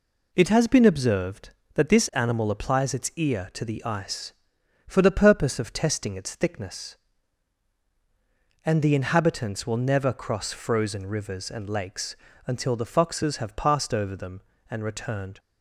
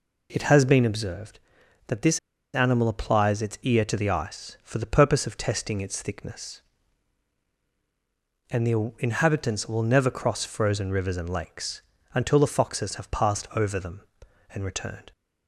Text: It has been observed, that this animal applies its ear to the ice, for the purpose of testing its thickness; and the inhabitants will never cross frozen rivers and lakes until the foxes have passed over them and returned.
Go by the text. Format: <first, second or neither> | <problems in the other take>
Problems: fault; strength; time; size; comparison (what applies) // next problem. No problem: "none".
first | pauses between "this" and "animal"; at 2.1 s; 0.36 s long // pauses between "lakes" and "until"; slight; at 11.8 s; 0.34 s long; slight in the first